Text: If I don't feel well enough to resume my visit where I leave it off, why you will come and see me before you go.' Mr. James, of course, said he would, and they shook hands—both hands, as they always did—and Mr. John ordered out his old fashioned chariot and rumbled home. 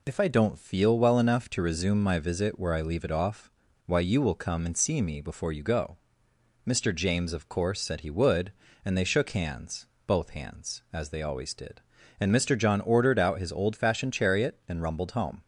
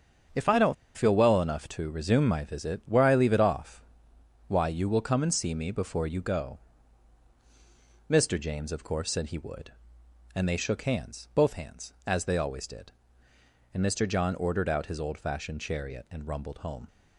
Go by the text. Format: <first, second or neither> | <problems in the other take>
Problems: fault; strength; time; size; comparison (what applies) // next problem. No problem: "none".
first | starts louder than the rest; strong; until 1.5 s; 7 dB // pauses between "don't" and "feel"; slight; at 0.7 s; 0.22 s long